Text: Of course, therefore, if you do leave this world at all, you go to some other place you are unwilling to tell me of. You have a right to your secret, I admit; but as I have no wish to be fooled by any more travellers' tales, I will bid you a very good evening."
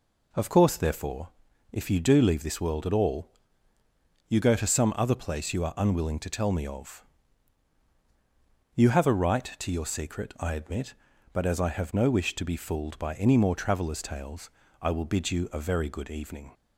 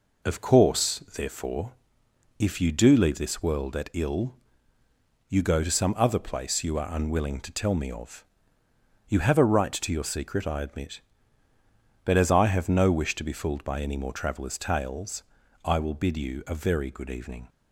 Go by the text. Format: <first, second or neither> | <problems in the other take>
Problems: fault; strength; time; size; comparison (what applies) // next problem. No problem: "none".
first | says "ill" for "all"; at 3.9 s